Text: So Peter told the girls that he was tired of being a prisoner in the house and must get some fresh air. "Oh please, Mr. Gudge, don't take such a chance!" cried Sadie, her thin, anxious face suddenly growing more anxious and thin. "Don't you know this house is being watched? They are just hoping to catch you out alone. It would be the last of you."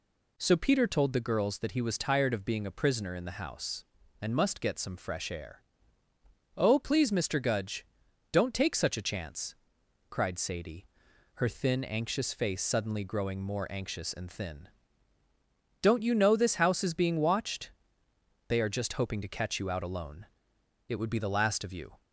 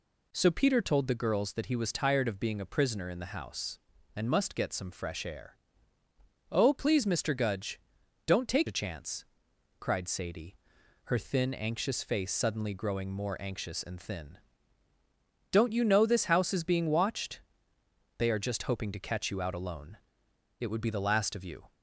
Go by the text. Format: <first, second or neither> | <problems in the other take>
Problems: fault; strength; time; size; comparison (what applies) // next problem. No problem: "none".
first | skips "such"; at 8.6 s